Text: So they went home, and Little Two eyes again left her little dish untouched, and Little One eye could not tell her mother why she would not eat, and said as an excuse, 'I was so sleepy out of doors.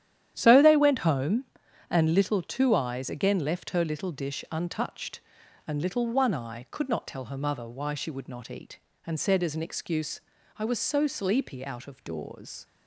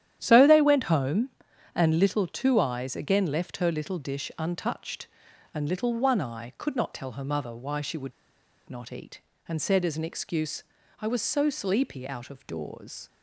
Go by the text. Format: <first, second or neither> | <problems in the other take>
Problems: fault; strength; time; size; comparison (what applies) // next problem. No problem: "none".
first | starts louder than the rest; strong; until 1.2 s; 11 dB; strong in the first // pauses between "would" and "not"; noticeable; at 8.1 s; 0.57 s long